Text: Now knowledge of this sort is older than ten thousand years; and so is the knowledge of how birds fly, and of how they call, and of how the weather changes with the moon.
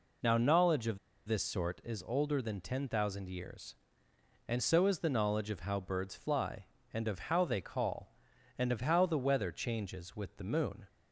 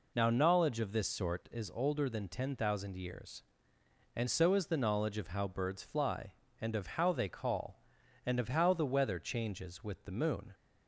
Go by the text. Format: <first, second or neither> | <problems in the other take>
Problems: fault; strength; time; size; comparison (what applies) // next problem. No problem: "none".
second | pauses between "of" and "this"; slight; at 0.9 s; 0.27 s long